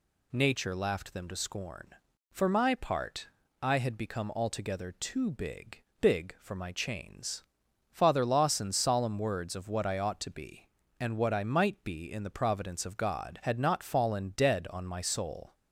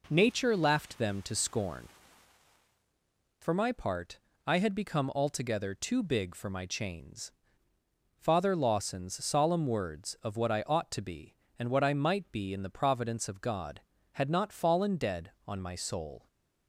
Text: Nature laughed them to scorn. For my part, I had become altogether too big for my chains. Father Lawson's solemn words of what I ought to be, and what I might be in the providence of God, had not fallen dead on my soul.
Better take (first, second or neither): second